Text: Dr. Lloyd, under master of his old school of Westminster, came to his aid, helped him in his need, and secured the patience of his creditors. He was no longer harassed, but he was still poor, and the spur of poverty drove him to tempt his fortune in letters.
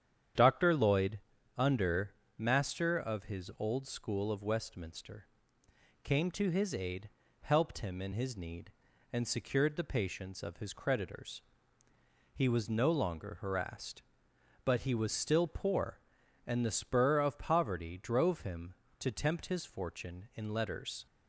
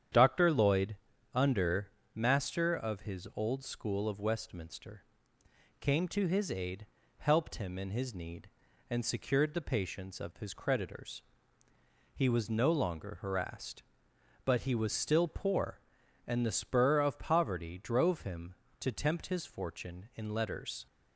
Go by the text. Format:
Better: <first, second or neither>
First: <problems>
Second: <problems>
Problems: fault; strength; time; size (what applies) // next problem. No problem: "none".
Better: neither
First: starts louder than the rest; strong; until 1.7 s; 9 dB // pauses between "under" and "master"; slight; at 2.1 s; 0.26 s long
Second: starts louder than the rest; strong; until 1.5 s; 9 dB // pauses between "under" and "master"; slight; at 1.8 s; 0.26 s long